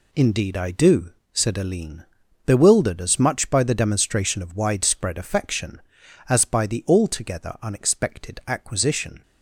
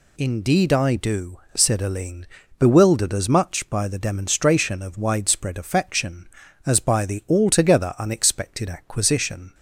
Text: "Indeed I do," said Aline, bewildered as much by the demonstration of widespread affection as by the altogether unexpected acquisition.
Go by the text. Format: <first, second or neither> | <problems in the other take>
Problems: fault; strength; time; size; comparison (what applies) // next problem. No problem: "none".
neither | none